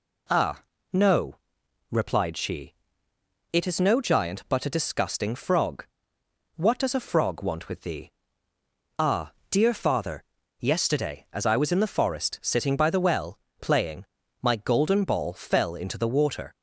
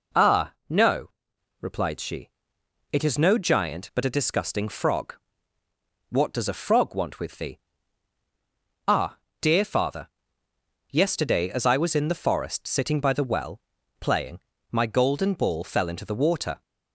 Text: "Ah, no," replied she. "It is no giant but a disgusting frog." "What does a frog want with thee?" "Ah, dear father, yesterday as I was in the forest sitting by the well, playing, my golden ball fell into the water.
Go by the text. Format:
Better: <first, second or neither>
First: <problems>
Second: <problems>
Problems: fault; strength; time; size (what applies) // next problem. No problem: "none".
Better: neither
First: none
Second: none